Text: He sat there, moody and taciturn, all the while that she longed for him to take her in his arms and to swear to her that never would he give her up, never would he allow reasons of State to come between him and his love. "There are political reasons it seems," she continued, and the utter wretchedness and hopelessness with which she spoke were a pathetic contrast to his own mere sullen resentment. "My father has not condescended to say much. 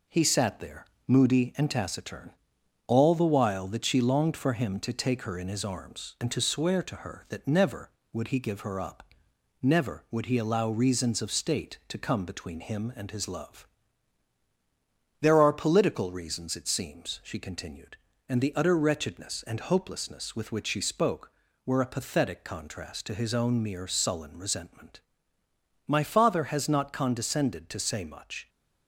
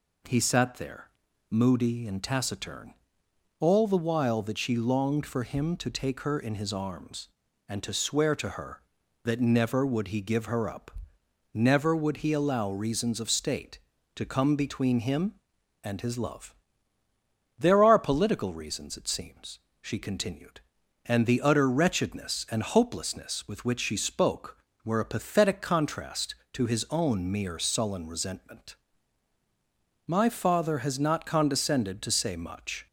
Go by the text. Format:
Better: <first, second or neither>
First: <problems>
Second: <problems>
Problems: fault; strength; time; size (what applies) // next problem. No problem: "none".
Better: second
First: gets quieter; throughout; 3.5 dB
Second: none